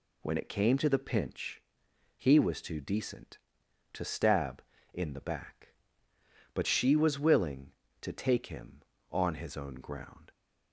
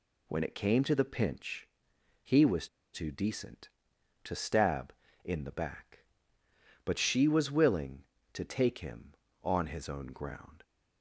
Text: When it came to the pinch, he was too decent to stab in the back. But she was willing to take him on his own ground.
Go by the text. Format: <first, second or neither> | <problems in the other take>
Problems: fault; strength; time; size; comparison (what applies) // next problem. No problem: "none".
first | pauses between "was" and "too"; slight; at 2.6 s; 0.26 s long